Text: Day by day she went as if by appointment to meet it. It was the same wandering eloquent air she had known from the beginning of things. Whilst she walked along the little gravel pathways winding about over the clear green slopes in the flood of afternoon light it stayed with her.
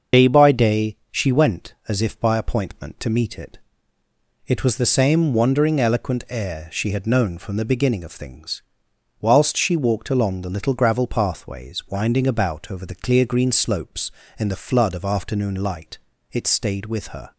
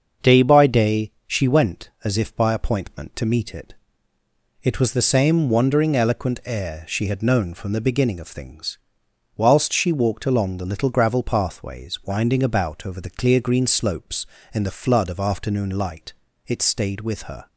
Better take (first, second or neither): second